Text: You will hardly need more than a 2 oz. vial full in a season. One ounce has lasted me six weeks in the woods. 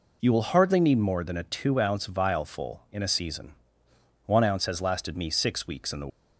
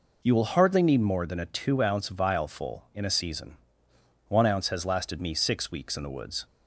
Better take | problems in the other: second | stops before "woods"; at 6.0 s

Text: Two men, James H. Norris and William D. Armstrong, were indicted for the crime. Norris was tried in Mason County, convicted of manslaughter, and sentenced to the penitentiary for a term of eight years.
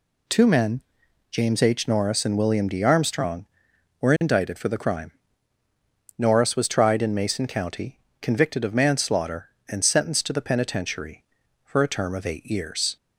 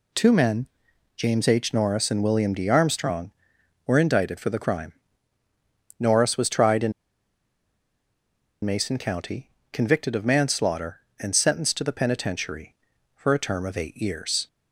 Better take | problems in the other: first | pauses between "in" and "Mason"; strong; at 6.9 s; 1.7 s long

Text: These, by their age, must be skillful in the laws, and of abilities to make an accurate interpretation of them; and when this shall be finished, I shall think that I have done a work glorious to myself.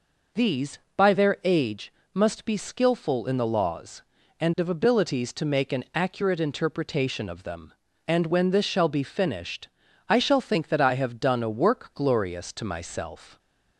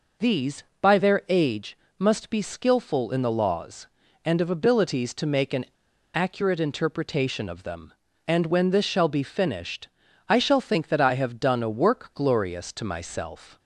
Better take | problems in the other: first | pauses between "an" and "accurate"; noticeable; at 5.6 s; 0.48 s long

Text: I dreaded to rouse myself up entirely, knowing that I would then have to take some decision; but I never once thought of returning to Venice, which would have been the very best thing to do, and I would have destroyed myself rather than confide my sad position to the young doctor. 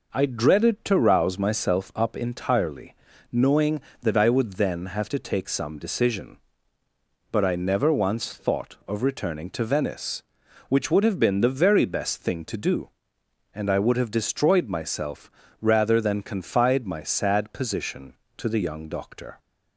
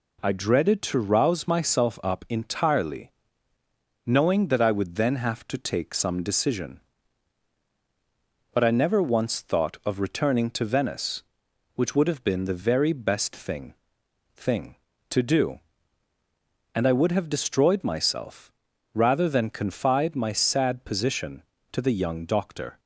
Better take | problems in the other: first | says "thing" twice; at 14.3 s // pauses between "myself" and "rather"; at 18.5 s; 0.42 s long; slight in the first

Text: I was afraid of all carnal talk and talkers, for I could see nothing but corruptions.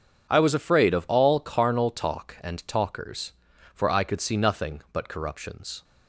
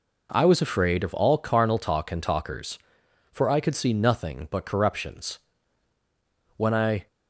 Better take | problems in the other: first | goes on to say "When I"; from 6.5 s on; 0.50 s long

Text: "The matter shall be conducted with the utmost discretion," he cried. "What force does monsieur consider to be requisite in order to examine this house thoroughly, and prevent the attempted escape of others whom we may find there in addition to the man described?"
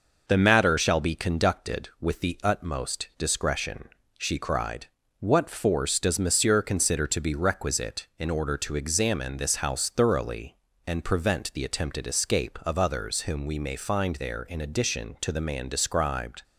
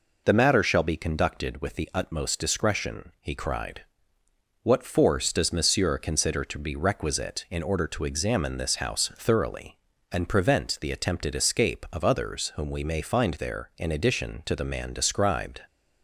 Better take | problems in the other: second | says "she" for "he"; at 4.1 s

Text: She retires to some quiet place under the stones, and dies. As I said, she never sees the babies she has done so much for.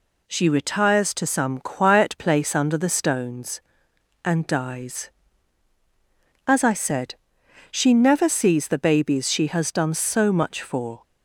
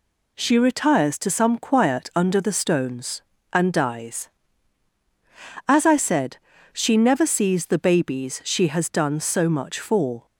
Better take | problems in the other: first | skips "place"; at 2.1 s

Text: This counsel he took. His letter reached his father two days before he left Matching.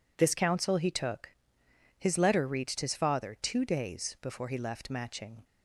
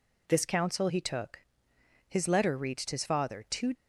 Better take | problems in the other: first | stops before "days before he left Matching"; at 3.7 s

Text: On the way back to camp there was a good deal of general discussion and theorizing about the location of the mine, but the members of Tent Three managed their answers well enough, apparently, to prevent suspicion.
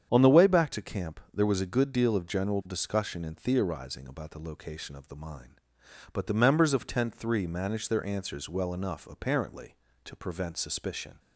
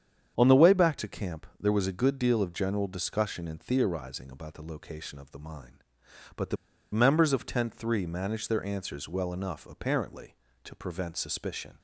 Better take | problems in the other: first | starts louder than the rest; strong; until 1.3 s; 8 dB; strong in the first // pauses between "camp" and "there"; slight; at 1.4 s; 0.16 s long; slight in the first // pauses between "the" and "members"; at 6.5 s; 0.36 s long

